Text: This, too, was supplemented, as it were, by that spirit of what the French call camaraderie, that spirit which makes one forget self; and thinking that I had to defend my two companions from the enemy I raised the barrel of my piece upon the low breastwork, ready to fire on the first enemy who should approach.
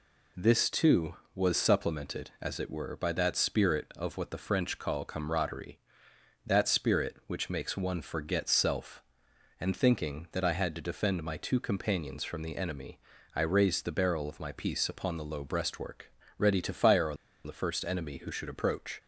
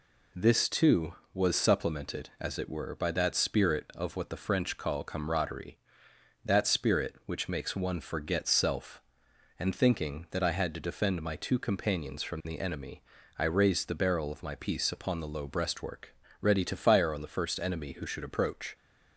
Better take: second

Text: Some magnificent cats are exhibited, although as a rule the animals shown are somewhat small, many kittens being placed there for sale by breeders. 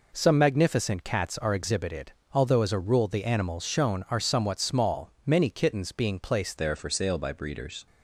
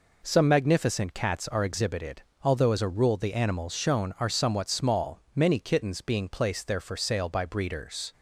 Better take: second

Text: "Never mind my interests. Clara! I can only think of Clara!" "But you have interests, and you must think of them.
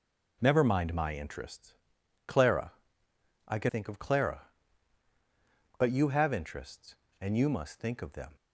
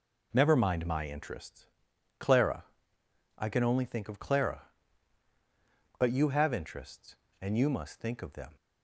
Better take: second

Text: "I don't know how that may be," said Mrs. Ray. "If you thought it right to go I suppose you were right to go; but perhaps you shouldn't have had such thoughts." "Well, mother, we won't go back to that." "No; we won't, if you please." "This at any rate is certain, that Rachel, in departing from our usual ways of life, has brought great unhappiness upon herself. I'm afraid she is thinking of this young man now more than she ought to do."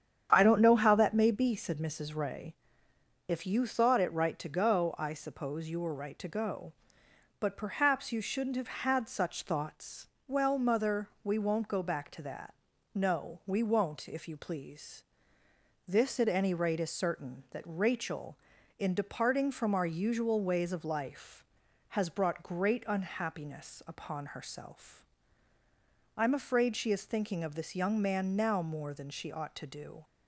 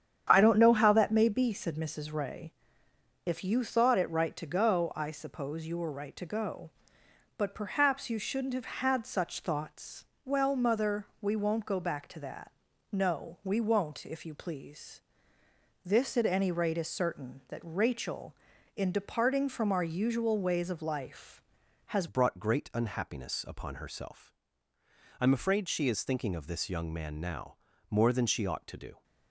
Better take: first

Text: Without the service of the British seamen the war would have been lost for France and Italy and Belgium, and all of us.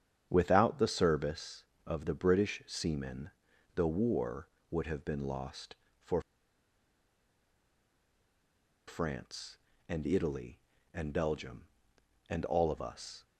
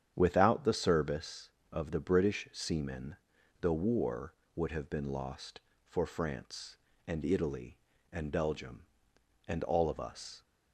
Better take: second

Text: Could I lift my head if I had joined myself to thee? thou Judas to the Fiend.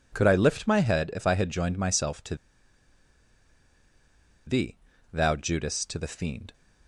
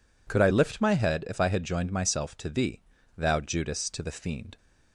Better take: second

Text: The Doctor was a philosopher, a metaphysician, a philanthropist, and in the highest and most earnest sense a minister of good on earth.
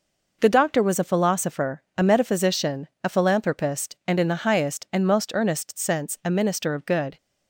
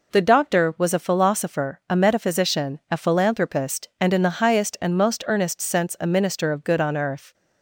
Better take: second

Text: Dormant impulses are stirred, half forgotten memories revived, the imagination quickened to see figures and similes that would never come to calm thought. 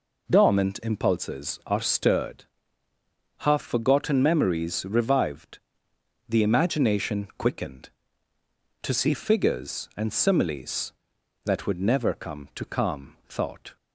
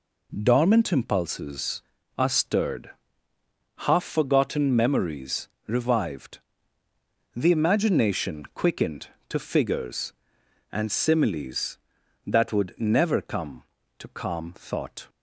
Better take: first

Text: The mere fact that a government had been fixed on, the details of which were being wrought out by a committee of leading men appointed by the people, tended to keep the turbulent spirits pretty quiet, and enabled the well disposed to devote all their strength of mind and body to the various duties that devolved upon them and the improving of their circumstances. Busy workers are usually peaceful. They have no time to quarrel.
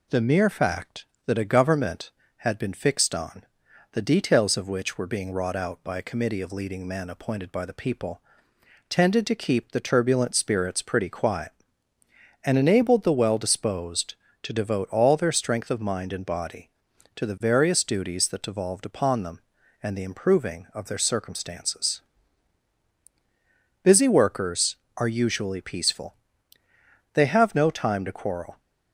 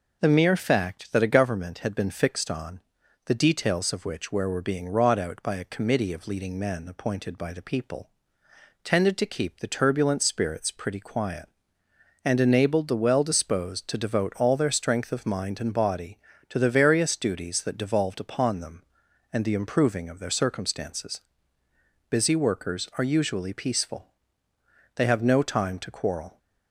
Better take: first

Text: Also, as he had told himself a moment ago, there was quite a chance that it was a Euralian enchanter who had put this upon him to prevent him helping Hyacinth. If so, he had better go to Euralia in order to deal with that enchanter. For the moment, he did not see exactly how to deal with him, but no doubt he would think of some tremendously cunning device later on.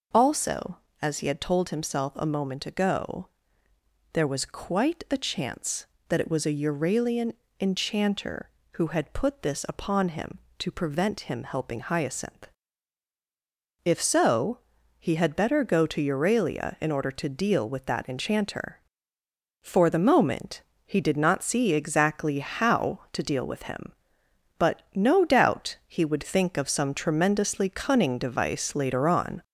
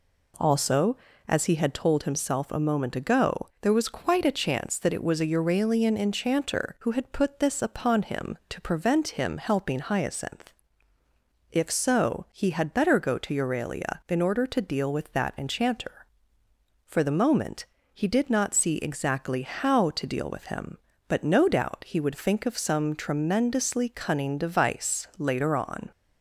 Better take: second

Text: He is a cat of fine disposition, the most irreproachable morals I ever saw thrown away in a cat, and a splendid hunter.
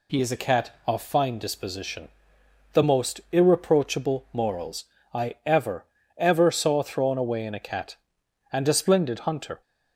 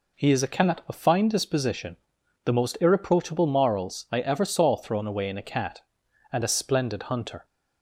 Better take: second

